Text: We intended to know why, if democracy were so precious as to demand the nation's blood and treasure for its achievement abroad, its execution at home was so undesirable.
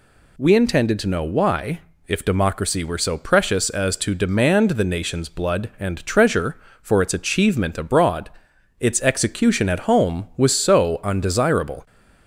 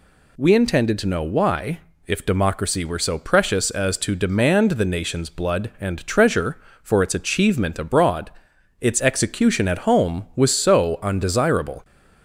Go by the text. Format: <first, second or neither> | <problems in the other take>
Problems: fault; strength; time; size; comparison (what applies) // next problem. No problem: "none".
neither | none